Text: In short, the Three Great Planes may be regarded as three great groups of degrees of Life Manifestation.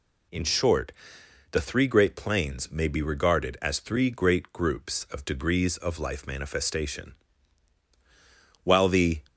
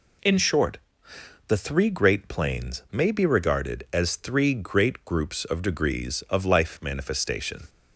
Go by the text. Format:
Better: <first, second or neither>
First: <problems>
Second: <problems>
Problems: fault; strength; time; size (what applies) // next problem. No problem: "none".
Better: second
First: goes on to say "While the"; from 8.6 s on; 0.58 s long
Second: none